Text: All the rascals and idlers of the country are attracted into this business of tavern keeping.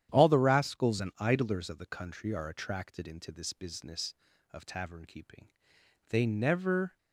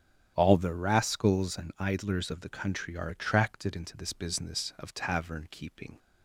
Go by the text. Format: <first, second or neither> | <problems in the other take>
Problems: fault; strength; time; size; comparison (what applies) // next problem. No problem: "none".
second | starts louder than the rest; strong; until 1.1 s; 10 dB; strong in the second // goes on to say "They never"; noticeable; from 6.0 s on; 0.88 s long